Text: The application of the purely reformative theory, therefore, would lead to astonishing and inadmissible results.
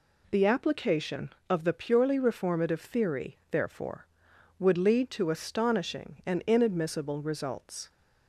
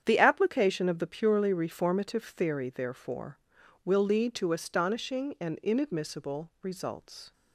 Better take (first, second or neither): first